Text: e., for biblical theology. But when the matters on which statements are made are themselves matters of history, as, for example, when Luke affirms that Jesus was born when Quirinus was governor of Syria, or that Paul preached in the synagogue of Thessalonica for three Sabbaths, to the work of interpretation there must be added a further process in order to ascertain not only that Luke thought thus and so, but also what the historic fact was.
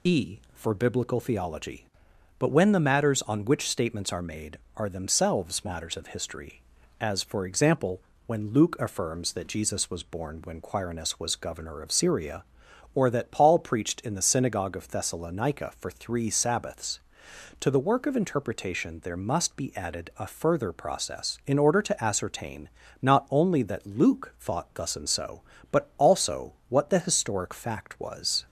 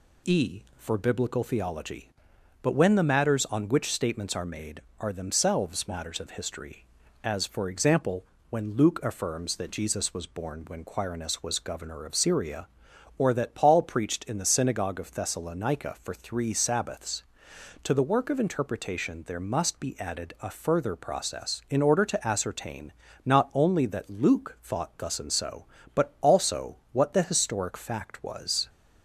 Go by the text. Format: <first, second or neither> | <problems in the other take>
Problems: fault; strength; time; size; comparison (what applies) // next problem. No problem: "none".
second | loses the start of "e"; at 0.0 s; 40 ms // pauses between "ascertain" and "not"; slight; at 22.6 s; 0.34 s long; slight in the second // pauses between "also" and "what"; slight; at 26.5 s; 0.16 s long; slight in the second